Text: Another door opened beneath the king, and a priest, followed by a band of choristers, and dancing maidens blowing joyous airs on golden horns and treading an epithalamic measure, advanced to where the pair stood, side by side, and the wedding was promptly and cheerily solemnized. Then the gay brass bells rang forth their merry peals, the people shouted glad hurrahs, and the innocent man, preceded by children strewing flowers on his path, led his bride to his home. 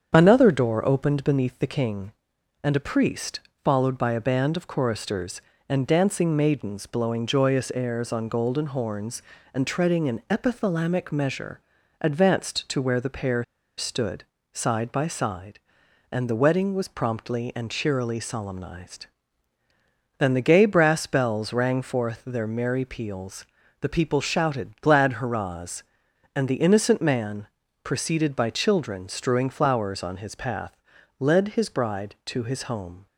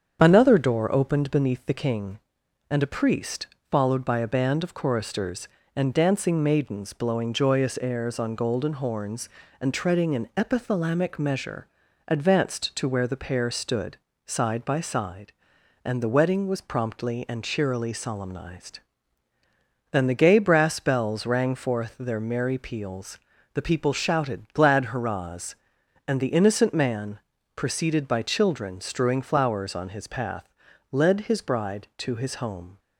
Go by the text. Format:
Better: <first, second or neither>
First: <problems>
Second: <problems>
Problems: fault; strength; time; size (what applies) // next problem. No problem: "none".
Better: second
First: starts louder than the rest; strong; until 1.1 s; 7.5 dB // pauses between "pair" and "stood"; slight; at 13.4 s; 0.33 s long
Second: starts louder than the rest; strong; until 1.2 s; 7.5 dB